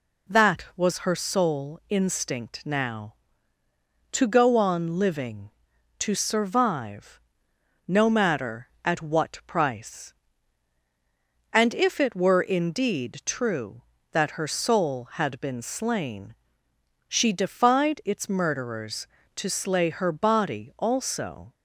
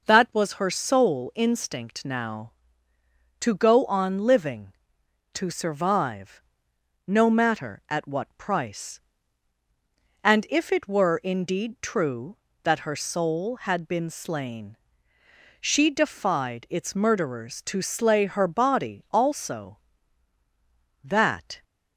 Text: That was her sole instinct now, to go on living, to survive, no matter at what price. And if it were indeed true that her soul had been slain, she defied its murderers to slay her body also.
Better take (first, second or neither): first